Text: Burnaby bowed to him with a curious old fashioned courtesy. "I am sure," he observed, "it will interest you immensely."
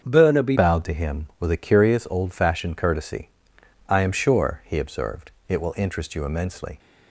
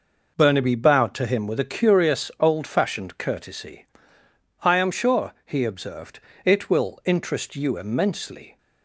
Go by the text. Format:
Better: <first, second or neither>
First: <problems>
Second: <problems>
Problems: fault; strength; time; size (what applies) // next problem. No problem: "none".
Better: second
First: starts louder than the rest; until 1.0 s; 6.5 dB // changes voice at "bowed"; from 0.5 s on; 6.2 s long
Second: none